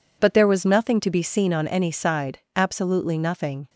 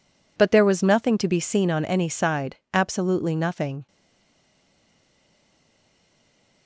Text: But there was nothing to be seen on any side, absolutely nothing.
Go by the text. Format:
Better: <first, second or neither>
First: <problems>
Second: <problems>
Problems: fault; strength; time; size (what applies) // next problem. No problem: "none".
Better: first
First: none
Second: stays silent after the last word; strong; from 3.8 s on; 2.8 s long